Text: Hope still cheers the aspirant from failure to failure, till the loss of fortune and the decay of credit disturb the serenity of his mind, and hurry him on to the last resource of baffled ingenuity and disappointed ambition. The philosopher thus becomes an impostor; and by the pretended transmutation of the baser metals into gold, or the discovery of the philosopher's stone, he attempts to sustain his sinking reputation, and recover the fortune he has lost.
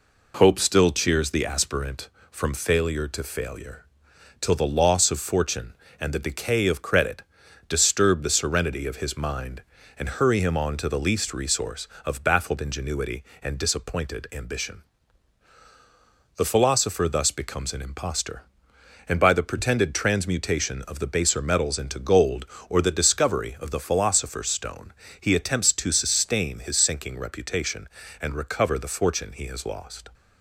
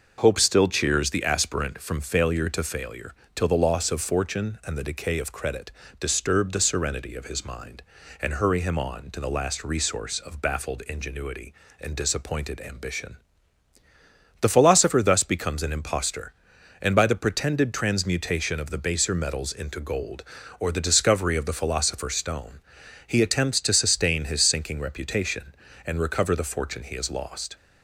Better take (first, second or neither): second